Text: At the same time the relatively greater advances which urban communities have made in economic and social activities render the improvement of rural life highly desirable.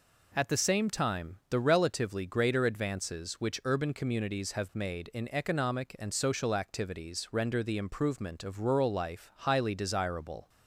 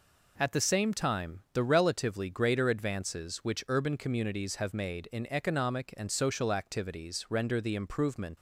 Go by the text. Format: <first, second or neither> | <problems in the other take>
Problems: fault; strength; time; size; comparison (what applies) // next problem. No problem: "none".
first | stops before "of rural life highly desirable"; at 8.3 s